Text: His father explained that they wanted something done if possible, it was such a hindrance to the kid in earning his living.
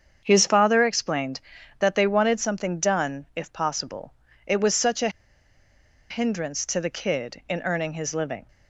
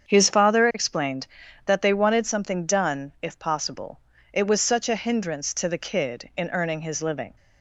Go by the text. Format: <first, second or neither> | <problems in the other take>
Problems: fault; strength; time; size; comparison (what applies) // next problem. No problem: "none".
second | starts louder than the rest; strong; until 1.2 s; 7.5 dB; strong in the second // pauses between "a" and "hindrance"; at 5.1 s; 0.99 s long